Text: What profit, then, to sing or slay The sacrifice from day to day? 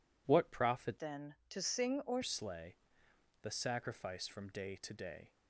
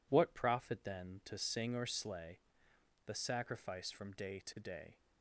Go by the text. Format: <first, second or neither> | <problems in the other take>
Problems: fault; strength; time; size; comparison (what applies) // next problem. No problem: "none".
second | changes voice from "then" to "or"; from 0.9 to 2.2 s; 1.3 s long // pauses between "slay" and "The"; noticeable; at 2.7 s; 0.68 s long; noticeable in the second